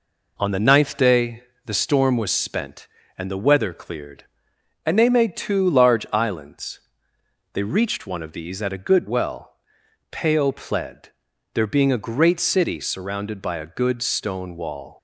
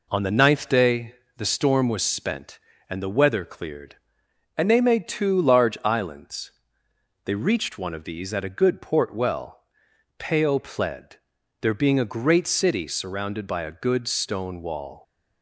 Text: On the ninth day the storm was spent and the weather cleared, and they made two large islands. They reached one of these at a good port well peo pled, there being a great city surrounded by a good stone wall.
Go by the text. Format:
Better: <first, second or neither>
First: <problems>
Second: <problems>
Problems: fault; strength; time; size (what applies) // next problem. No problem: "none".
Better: second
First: pauses between "day" and "the"; slight; at 1.4 s; 0.20 s long // skips "port"; at 9.0 s // pauses between "well" and "peo"; noticeable; at 9.4 s; 0.62 s long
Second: pauses between "day" and "the"; slight; at 1.1 s; 0.20 s long // pauses between "well" and "peo"; noticeable; at 9.5 s; 0.62 s long